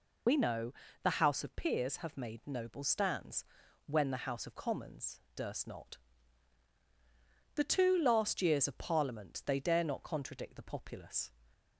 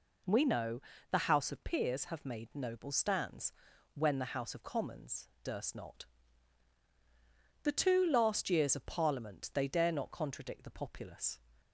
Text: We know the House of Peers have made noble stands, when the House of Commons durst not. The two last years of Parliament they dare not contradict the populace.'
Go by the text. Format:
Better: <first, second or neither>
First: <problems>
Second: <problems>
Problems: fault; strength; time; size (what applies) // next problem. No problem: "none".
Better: second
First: loses the start of "We"; at 0.2 s; 95 ms // pauses between "know" and "the"; slight; at 0.7 s; 0.30 s long // pauses between "Commons" and "durst"; slight; at 5.1 s; 0.16 s long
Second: pauses between "know" and "the"; slight; at 0.8 s; 0.30 s long // pauses between "Commons" and "durst"; slight; at 5.2 s; 0.16 s long